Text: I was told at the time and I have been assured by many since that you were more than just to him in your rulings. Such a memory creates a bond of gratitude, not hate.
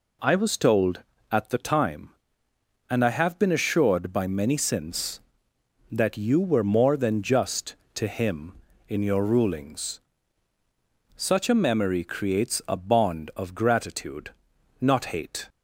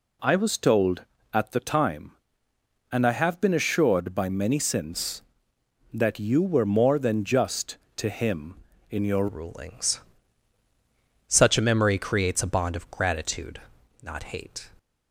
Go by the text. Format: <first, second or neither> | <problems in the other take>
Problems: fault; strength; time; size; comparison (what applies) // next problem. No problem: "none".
first | changes voice at "rulings"; from 9.2 s on; 5.4 s long